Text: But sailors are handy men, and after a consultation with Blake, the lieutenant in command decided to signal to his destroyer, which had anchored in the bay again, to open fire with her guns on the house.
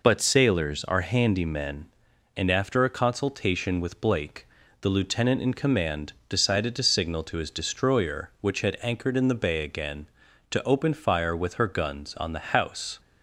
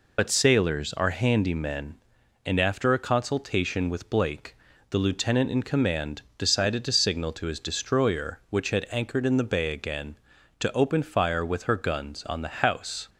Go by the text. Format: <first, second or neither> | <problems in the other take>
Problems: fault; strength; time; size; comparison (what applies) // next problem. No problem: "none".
first | loses the start of "But"; at 0.1 s; 55 ms // pauses between "command" and "decided"; slight; at 6.2 s; 0.16 s long; slight in the first